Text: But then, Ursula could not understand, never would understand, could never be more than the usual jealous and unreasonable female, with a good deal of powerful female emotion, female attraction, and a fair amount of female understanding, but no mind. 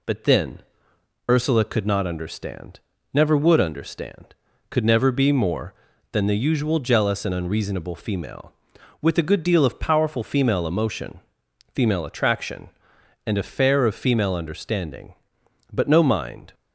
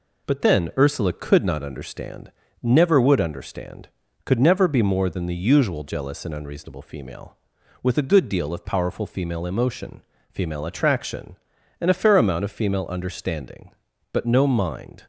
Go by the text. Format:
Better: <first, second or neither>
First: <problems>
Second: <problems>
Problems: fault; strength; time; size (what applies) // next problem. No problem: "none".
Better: second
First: skips "amount"; at 13.8 s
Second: none